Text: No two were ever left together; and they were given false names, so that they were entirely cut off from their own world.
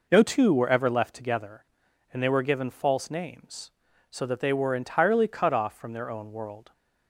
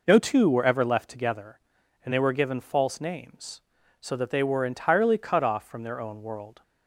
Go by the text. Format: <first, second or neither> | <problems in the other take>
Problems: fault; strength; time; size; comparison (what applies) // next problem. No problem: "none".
neither | none